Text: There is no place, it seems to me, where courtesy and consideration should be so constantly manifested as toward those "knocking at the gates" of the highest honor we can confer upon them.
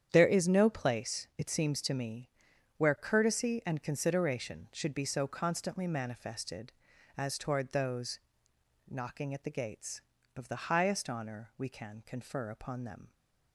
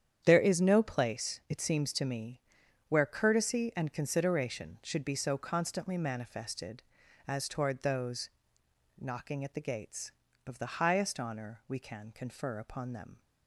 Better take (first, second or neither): neither